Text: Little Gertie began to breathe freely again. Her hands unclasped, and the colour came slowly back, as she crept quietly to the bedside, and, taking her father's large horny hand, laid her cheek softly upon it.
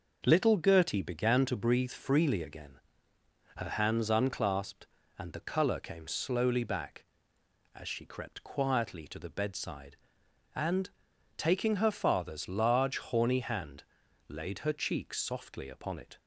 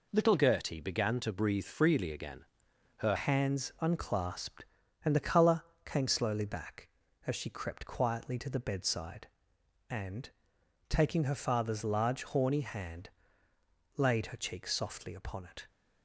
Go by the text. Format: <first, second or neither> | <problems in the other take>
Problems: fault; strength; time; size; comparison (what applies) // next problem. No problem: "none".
first | changes voice at "hands"; from 3.1 s on; 12.5 s long // pauses between "colour" and "came"; slight; at 5.6 s; 0.24 s long